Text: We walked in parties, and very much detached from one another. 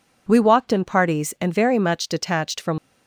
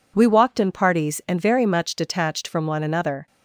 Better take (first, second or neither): second